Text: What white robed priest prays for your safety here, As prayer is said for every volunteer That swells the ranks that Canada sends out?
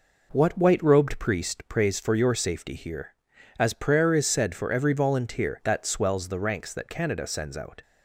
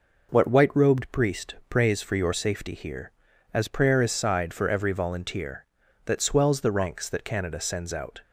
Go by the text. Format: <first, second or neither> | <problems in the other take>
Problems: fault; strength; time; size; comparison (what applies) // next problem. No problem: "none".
first | says "sighed" for "said"; at 4.1 s